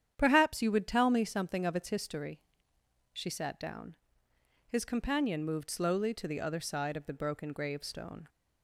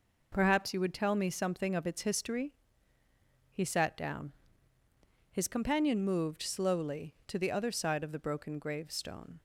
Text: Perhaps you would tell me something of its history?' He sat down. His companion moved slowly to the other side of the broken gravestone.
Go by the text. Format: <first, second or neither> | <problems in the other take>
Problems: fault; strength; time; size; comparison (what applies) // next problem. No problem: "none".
second | starts louder than the rest; strong; until 1.1 s; 9.5 dB // says "She" for "He"; at 3.1 s